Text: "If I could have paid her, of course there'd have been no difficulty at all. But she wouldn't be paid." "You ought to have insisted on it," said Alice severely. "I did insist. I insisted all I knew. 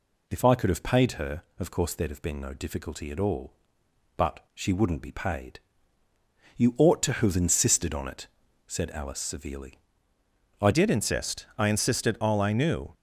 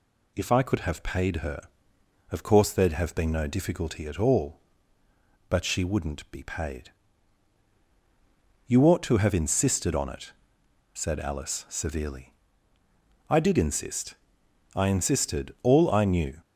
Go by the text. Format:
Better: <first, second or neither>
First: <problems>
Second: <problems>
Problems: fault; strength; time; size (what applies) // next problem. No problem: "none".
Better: second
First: changes voice at "did"; from 10.7 s on; 2.2 s long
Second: none